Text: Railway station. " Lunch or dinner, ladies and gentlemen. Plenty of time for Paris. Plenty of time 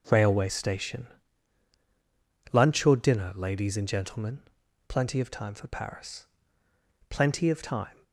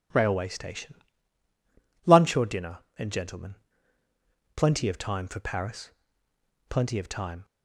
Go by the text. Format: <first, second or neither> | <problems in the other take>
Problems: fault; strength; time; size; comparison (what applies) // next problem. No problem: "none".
first | skips "ladies"; at 2.8 s